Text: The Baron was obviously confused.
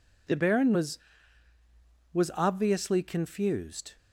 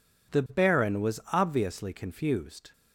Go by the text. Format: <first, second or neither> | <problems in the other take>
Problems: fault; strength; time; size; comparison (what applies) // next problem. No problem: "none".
second | says "was" twice; at 2.1 s